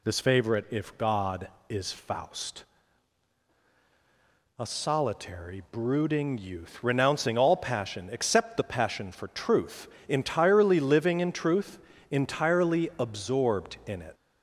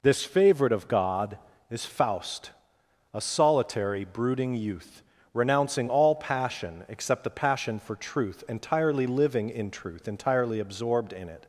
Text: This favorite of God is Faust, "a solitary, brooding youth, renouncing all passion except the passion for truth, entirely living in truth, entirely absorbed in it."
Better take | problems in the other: second | says "if" for "of"; at 0.6 s

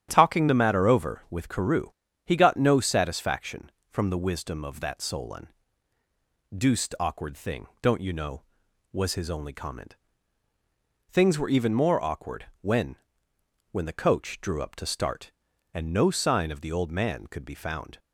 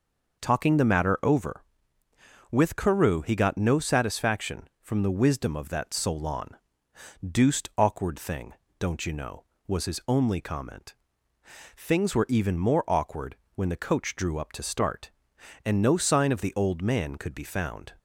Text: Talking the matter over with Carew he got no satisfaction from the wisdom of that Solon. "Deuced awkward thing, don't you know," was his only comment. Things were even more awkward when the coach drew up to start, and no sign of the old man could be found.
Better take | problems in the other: second | starts louder than the rest; strong; until 1.1 s; 10 dB // pauses between "Carew" and "he"; slight; at 1.9 s; 0.34 s long // pauses between "awkward" and "when"; slight; at 12.4 s; 0.16 s long; slight in the second // says "when" twice; at 13.7 s

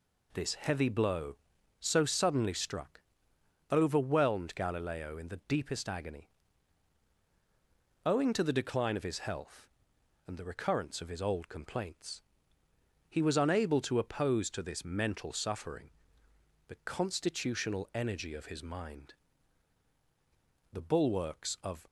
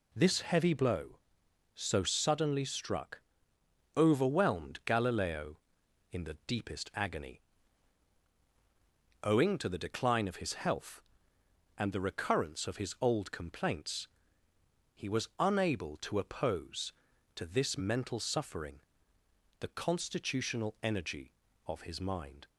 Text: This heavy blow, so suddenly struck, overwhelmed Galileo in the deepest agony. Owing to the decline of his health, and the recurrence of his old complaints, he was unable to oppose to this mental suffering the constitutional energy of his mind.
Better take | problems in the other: second | pauses between "suffering" and "the"; noticeable; at 15.8 s; 0.80 s long; noticeable in the second // goes on to say "The bulwarks of"; noticeable; from 20.7 s on; 1.1 s long

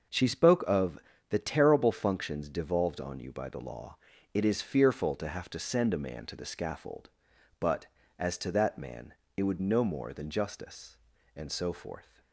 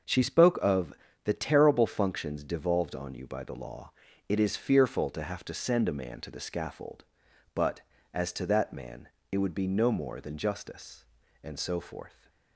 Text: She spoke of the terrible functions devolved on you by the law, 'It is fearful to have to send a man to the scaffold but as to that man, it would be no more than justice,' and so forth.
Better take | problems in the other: second | starts louder than the rest; until 1.4 s; 6 dB; also in the second // pauses between "of" and "the"; slight; at 0.9 s; 0.32 s long; slight in the second // skips "be"; at 9.5 s

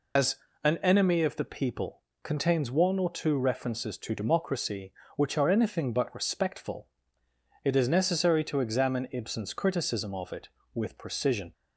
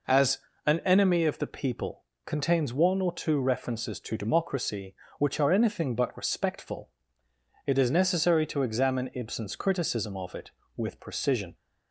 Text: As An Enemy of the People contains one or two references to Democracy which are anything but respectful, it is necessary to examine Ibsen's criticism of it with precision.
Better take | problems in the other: second | loses the start of "As"; at 0.1 s; 110 ms // pauses between "As" and "An"; slight; at 0.3 s; 0.28 s long; slight in the second // pauses between "People" and "contains"; slight; at 2.0 s; 0.22 s long; slight in the second

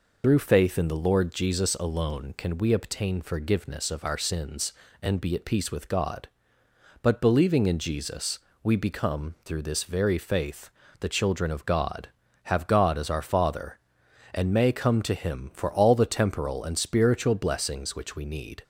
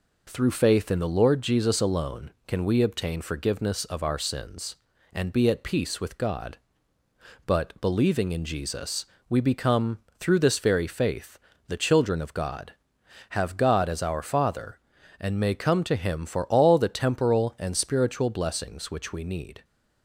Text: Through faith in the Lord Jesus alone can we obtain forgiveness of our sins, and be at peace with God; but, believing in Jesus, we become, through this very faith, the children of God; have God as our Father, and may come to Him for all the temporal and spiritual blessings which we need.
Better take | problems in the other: second | loses the start of "Through"; at 0.2 s; 50 ms

